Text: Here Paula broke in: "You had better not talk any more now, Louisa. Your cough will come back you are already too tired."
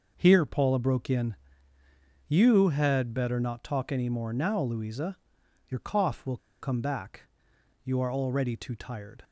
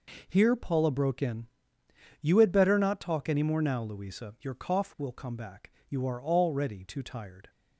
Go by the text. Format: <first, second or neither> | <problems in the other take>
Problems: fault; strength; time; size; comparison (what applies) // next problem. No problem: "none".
second | pauses between "will" and "come"; slight; at 6.3 s; 0.24 s long // pauses between "back" and "you"; noticeable; at 7.2 s; 0.66 s long; slight in the second